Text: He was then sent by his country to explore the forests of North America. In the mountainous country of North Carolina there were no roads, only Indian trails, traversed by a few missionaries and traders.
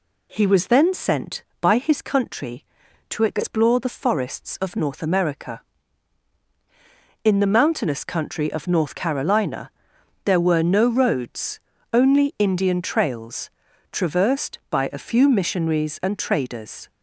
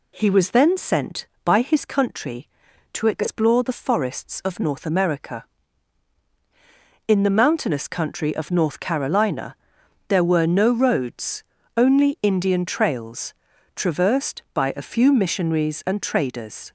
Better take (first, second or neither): neither